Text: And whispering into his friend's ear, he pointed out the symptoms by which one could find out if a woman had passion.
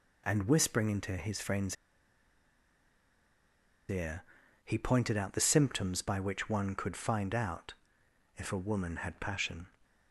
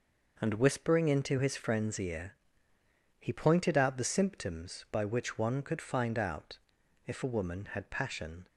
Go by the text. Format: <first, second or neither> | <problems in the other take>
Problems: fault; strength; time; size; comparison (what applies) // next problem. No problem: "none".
second | pauses between "friend's" and "ear"; strong; at 1.7 s; 2.1 s long // pauses between "out" and "if"; noticeable; at 7.7 s; 0.64 s long; noticeable in the second